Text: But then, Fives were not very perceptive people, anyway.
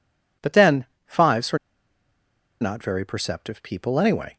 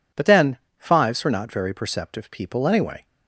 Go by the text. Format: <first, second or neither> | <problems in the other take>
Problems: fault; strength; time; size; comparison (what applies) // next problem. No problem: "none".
second | pauses between "were" and "not"; at 1.5 s; 1.0 s long